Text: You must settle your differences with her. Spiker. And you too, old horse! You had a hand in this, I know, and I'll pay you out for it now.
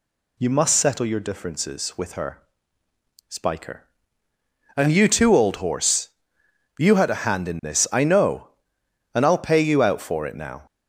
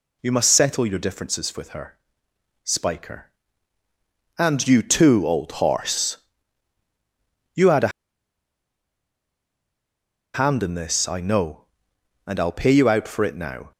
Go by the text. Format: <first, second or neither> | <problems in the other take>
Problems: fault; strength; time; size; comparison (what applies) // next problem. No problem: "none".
first | pauses between "a" and "hand"; strong; at 7.8 s; 2.4 s long